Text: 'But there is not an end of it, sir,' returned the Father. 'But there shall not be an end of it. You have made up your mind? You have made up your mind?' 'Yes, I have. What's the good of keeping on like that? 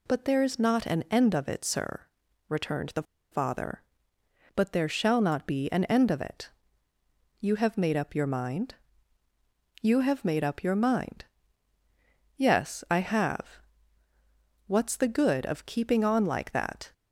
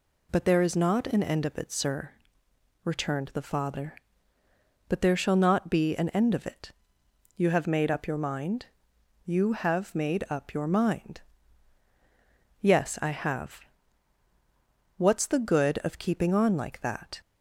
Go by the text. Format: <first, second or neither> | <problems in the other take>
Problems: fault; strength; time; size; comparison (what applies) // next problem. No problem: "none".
second | pauses between "the" and "Father"; slight; at 3.0 s; 0.28 s long